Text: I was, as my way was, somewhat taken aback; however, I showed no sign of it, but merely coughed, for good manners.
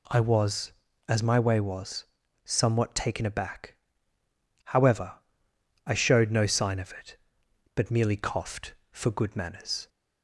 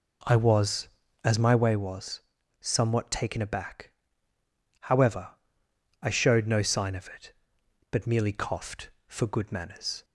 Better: first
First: none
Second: starts louder than the rest; until 1.7 s; 3.5 dB

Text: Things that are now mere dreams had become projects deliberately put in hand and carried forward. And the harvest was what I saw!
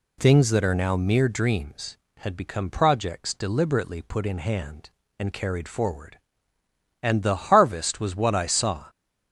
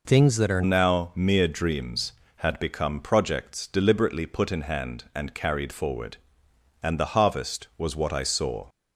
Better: first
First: none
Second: changes voice at "now"; from 0.6 s on; 8.0 s long

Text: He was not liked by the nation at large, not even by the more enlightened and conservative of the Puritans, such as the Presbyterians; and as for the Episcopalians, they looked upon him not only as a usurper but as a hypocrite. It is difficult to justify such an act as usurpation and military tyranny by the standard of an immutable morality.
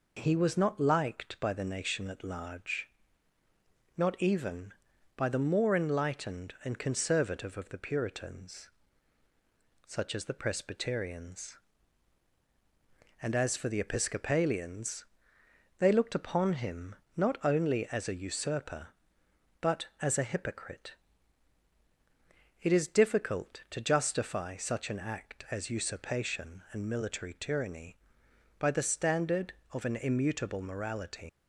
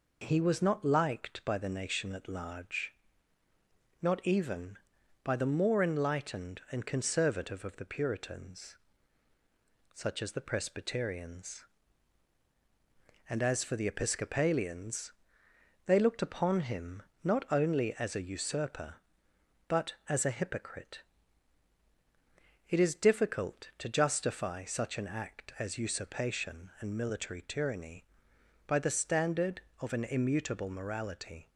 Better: second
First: pauses between "him" and "not"; slight; at 16.9 s; 0.20 s long // leaves "morality" unfinished; at 31.2 s; 110 ms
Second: pauses between "him" and "not"; slight; at 17.0 s; 0.20 s long

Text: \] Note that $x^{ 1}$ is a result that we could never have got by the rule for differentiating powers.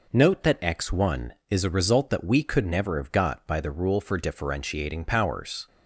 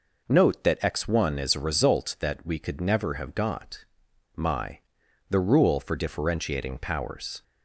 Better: first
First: none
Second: says "my" for "by"; at 4.3 s

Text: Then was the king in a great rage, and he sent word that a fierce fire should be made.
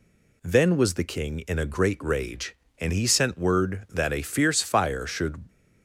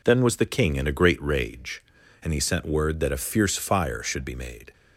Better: second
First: stops before "be made"; at 5.4 s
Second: none

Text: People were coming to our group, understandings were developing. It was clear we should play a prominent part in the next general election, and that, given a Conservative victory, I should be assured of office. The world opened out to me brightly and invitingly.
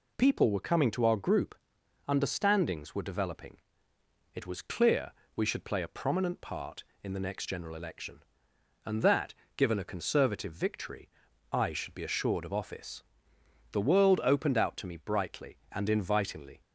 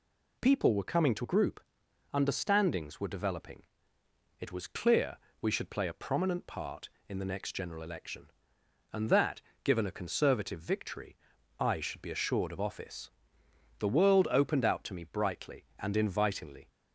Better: first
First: pauses between "clear" and "we"; slight; at 5.1 s; 0.24 s long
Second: skips "our"; at 1.2 s // pauses between "clear" and "we"; slight; at 5.1 s; 0.24 s long

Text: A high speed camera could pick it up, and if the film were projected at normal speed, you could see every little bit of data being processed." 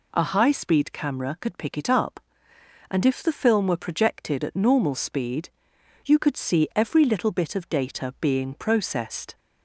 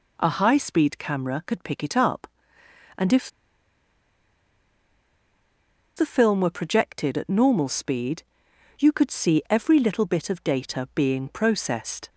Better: first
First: none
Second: pauses between "if" and "the"; strong; at 3.2 s; 2.6 s long

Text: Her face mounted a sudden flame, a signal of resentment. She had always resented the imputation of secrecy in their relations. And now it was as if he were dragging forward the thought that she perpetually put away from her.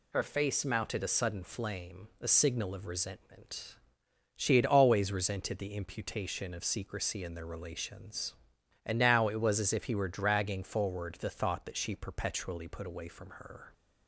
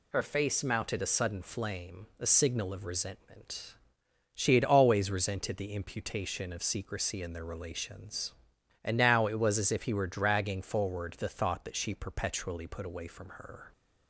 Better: neither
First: none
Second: none

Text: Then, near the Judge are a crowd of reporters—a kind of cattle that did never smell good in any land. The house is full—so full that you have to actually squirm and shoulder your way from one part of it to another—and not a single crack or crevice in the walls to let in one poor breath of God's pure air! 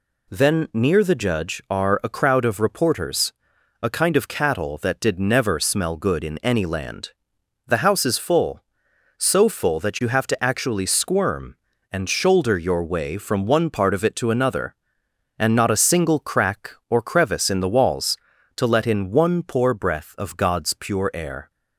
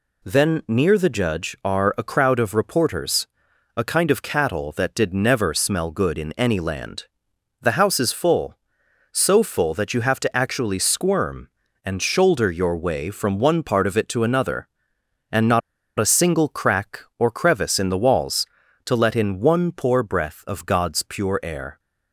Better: first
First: none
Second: pauses between "not" and "a"; at 15.6 s; 0.38 s long

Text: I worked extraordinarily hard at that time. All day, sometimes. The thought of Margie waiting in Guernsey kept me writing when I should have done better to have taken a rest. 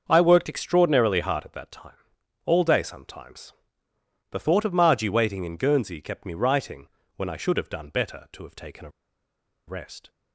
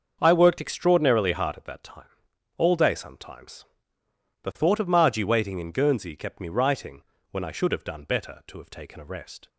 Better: second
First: starts louder than the rest; until 1.1 s; 6.5 dB // pauses between "writing" and "when"; slight; at 6.8 s; 0.28 s long // pauses between "a" and "rest"; noticeable; at 8.8 s; 0.78 s long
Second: starts louder than the rest; until 1.2 s; 6.5 dB // pauses between "writing" and "when"; slight; at 7.0 s; 0.28 s long

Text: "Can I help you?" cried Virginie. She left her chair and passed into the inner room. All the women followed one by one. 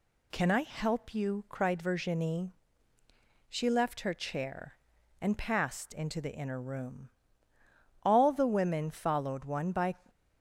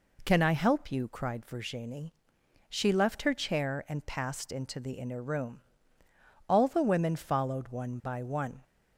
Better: second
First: stops before "one"; at 10.0 s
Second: none

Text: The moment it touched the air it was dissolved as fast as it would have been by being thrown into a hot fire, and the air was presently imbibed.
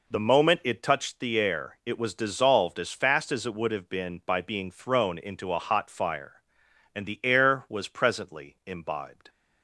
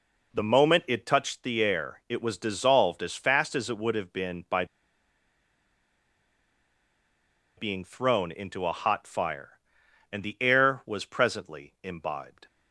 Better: first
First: none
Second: pauses between "by" and "being"; strong; at 4.6 s; 2.9 s long

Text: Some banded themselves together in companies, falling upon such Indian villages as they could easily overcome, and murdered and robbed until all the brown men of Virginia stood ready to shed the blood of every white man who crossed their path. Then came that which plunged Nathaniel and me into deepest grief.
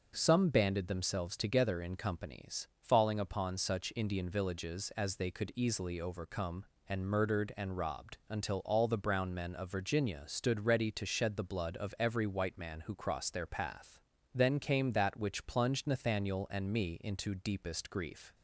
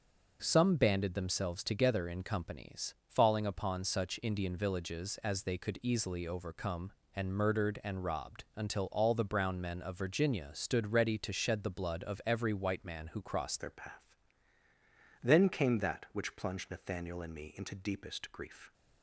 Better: first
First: none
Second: changes voice at "their"; from 13.5 s on; 5.2 s long

